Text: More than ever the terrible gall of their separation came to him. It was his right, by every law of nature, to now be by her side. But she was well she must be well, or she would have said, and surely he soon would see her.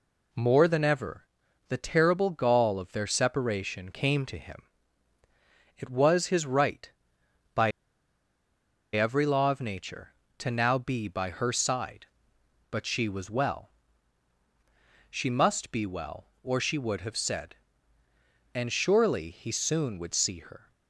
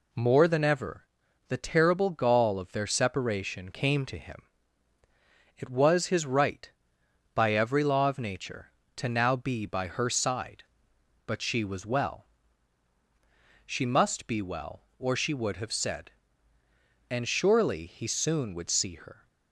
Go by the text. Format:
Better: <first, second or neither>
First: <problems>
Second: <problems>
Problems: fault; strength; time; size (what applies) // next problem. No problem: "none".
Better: second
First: pauses between "ever" and "the"; at 1.2 s; 0.40 s long // pauses between "by" and "every"; at 7.7 s; 1.2 s long // pauses between "well" and "she"; strong; at 13.6 s; 1.4 s long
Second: pauses between "ever" and "the"; at 1.0 s; 0.40 s long // pauses between "well" and "she"; strong; at 12.2 s; 1.4 s long